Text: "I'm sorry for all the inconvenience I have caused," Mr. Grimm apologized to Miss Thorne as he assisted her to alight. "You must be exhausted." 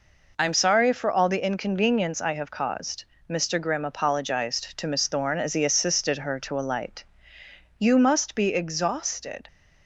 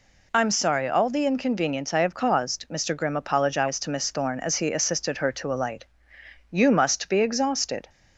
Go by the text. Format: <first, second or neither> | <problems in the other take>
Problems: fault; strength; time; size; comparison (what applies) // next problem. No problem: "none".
first | skips "for"; at 0.8 s